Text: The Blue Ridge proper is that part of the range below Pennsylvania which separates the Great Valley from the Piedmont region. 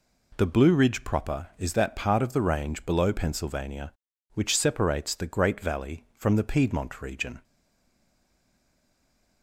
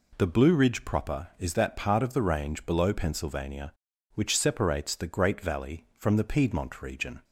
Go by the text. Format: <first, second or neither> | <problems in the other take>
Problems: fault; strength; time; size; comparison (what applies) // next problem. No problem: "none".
second | stays silent after the last word; noticeable; from 7.4 s on; 2.0 s long